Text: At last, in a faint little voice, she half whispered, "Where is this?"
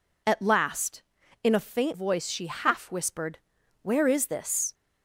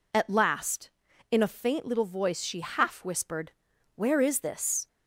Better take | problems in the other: second | skips "little"; at 1.9 s

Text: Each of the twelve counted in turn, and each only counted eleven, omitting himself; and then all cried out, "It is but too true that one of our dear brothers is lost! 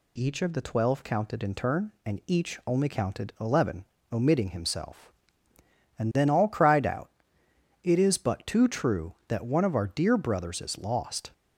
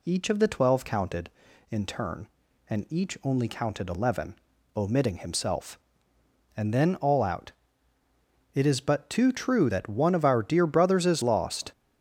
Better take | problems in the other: first | skips "cried"; at 7.2 s

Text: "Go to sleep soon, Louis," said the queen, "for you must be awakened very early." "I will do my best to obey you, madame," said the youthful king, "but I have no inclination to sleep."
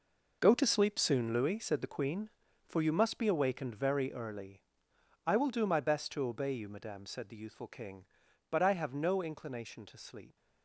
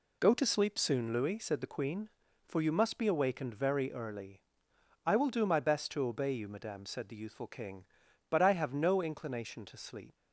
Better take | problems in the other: second | gets quieter; strong; throughout; 12 dB

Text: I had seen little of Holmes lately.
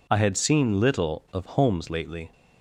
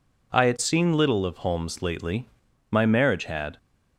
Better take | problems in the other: first | goes on to say "My marriage had"; noticeable; from 2.6 s on; 0.88 s long

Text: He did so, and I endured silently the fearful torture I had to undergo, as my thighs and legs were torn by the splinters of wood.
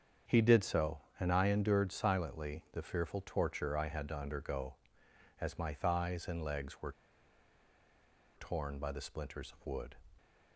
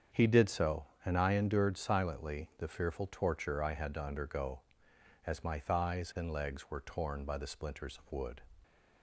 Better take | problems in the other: second | starts louder than the rest; strong; until 1.4 s; 7.5 dB; strong in the second // pauses between "were" and "torn"; strong; at 6.9 s; 1.4 s long

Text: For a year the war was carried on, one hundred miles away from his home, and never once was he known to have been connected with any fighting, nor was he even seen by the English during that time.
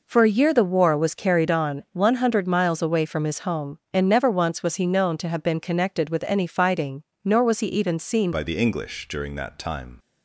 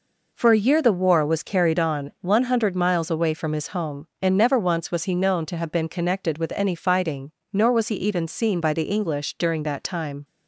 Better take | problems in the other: second | changes voice at "by"; from 8.3 s on; 1.6 s long

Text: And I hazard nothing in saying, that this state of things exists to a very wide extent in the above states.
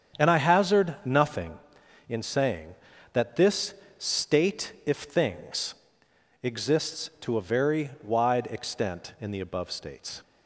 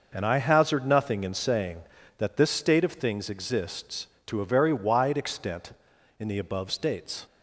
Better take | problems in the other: second | starts louder than the rest; strong; until 1.2 s; 8 dB // pauses between "this" and "state"; slight; at 3.7 s; 0.22 s long // says "if" for "of"; at 4.8 s // pauses between "things" and "exists"; noticeable; at 5.7 s; 0.68 s long

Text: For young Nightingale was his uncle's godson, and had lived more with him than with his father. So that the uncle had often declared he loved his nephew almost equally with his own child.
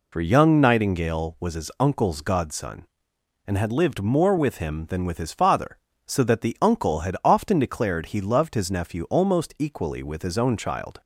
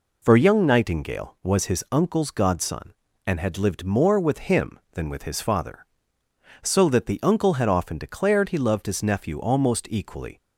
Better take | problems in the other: first | stops before "with his own child"; at 10.3 s

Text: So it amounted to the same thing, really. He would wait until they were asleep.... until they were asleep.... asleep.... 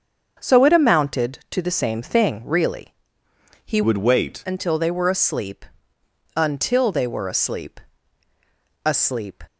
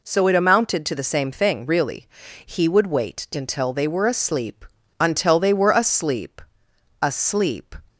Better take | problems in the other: second | starts louder than the rest; until 1.3 s; 7 dB // changes voice from "would" to "wait"; from 3.8 to 4.4 s; 0.6 s long

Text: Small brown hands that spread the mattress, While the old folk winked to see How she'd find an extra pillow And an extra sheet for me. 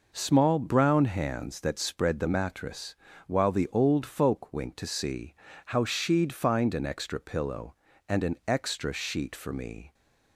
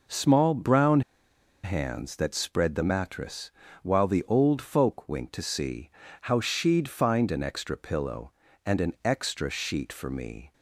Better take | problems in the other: first | pauses between "brown" and "hands"; noticeable; at 1.0 s; 0.63 s long // pauses between "see" and "How"; slight; at 5.8 s; 0.34 s long; slight in the first

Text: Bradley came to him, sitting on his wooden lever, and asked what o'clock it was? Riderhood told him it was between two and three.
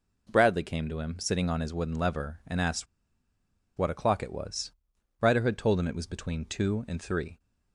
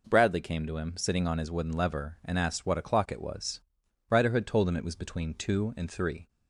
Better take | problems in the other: second | pauses between "asked" and "what"; noticeable; at 2.8 s; 0.92 s long

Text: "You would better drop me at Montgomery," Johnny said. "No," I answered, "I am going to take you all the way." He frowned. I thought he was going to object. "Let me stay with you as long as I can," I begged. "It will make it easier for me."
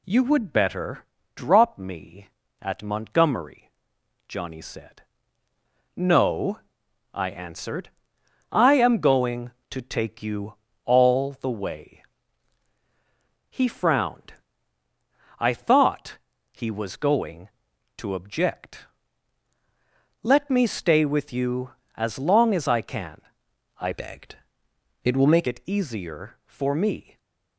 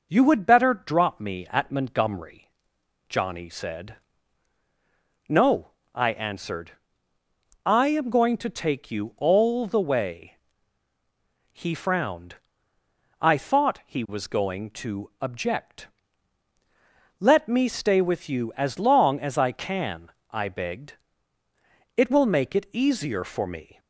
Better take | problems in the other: second | pauses between "better" and "drop"; slight; at 1.0 s; 0.30 s long // pauses between "you" and "all"; slight; at 10.5 s; 0.28 s long // pauses between "thought" and "he"; slight; at 16.1 s; 0.32 s long // changes voice from "begged" to "make"; from 23.9 to 25.4 s; 1.5 s long

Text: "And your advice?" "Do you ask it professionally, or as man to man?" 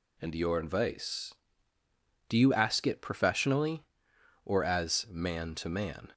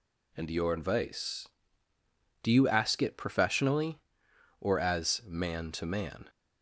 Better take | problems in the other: neither | none

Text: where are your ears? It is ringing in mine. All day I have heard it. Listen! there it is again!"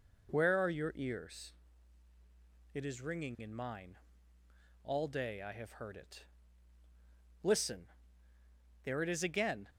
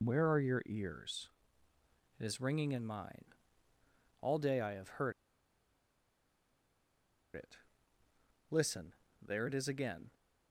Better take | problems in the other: first | pauses between "heard" and "it"; strong; at 5.1 s; 2.2 s long

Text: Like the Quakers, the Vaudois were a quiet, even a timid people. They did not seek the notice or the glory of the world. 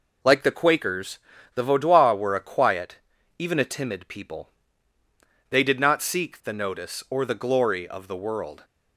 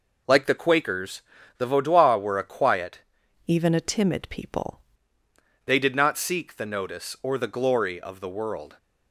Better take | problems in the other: first | changes voice from "even" to "people"; from 3.4 to 4.7 s; 1.3 s long

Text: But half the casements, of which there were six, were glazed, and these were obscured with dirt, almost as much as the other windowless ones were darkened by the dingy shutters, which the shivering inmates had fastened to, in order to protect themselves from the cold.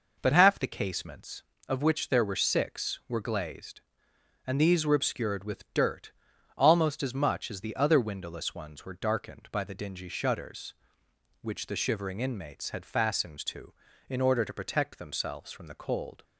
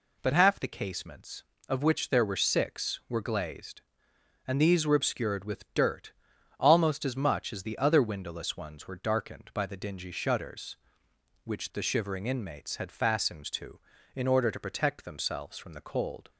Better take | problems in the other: second | starts louder than the rest; noticeable; until 1.4 s; 5 dB

